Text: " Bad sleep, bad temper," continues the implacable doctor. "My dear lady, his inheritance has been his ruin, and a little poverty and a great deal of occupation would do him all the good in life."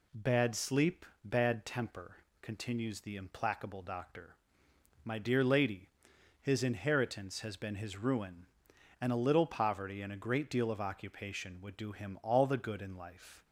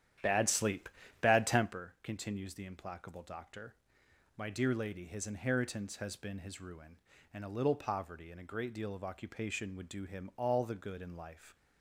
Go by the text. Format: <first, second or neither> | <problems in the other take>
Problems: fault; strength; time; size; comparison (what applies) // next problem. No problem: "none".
first | starts louder than the rest; strong; until 1.9 s; 10.5 dB